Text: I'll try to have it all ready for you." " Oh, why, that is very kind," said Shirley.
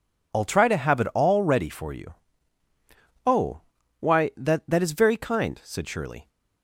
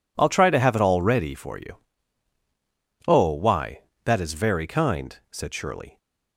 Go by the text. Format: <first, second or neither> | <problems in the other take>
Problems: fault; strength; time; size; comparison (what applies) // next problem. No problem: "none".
second | says "that" twice; at 4.6 s